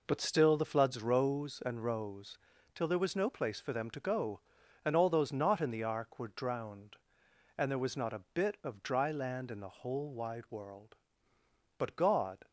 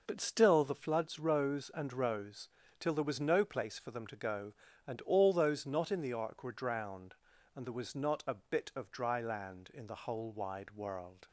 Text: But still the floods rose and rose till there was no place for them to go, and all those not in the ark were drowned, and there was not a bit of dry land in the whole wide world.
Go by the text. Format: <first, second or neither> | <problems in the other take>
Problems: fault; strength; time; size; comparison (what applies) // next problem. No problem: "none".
second | pauses between "rose" and "till"; slight; at 2.3 s; 0.36 s long; slight in the second // goes on to say "But God"; noticeable; from 11.7 s on; 0.70 s long